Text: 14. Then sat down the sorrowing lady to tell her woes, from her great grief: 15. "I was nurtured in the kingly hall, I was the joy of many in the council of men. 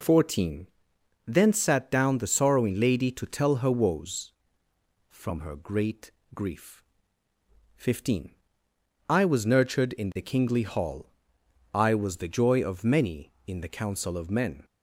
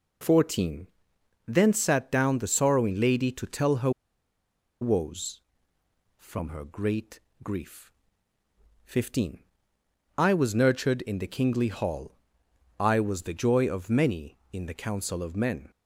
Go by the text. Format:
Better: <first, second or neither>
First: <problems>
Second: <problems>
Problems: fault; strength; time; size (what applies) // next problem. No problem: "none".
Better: first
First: pauses between "great" and "grief"; slight; at 6.0 s; 0.24 s long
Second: pauses between "her" and "woes"; noticeable; at 3.8 s; 0.91 s long // pauses between "great" and "grief"; slight; at 7.1 s; 0.24 s long